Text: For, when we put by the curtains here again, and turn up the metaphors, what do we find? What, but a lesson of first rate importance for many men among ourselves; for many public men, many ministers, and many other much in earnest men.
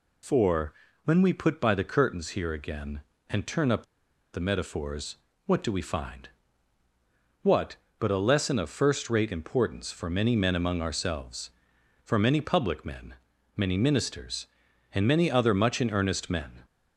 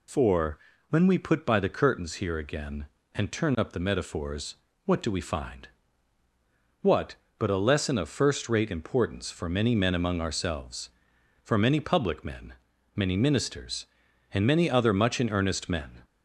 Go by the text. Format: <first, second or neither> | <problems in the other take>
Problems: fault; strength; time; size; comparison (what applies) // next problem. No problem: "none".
second | pauses between "up" and "the"; noticeable; at 3.8 s; 0.49 s long